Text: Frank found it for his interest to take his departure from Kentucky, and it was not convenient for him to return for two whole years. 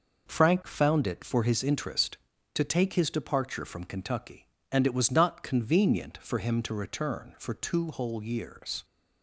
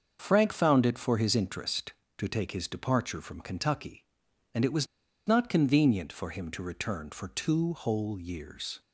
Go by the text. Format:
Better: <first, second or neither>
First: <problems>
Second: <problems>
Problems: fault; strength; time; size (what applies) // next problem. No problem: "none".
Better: first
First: none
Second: starts louder than the rest; until 1.2 s; 6.5 dB // pauses between "was" and "not"; at 4.8 s; 0.40 s long